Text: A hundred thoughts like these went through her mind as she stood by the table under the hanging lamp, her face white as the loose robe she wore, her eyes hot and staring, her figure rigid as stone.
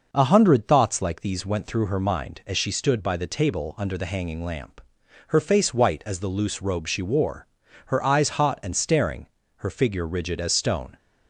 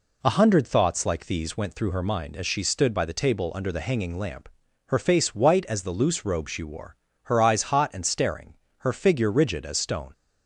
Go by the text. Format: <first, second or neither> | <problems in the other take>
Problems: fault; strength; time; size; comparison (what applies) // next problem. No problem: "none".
neither | none